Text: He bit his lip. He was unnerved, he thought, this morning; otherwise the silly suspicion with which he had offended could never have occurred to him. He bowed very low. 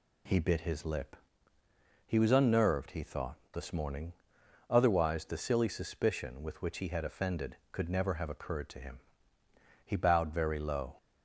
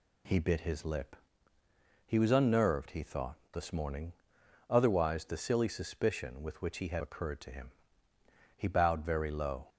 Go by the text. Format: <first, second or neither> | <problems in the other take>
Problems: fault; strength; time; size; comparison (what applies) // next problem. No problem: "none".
first | skips "offended could never have"; at 7.0 s